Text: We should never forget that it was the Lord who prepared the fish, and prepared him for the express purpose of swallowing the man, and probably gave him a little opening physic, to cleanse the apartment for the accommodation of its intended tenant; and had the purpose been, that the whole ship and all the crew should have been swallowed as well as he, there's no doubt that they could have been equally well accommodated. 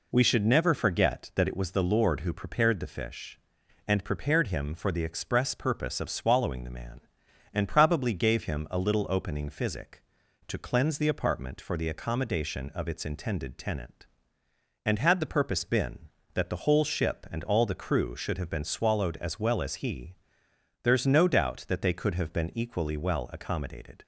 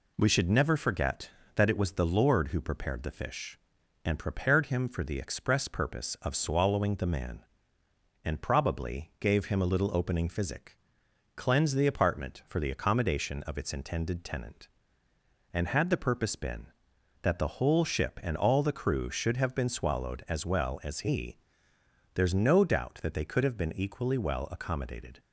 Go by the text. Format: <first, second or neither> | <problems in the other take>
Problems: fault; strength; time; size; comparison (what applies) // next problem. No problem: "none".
first | skips "to"; at 11.0 s